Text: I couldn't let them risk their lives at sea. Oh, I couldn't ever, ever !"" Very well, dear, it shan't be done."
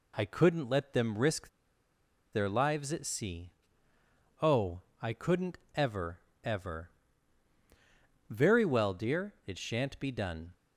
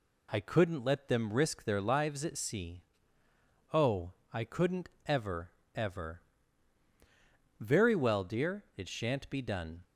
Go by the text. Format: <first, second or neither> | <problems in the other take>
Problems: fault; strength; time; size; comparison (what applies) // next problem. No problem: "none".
second | pauses between "risk" and "their"; noticeable; at 1.4 s; 0.84 s long // pauses between "couldn't" and "ever"; slight; at 5.5 s; 0.18 s long; slight in the second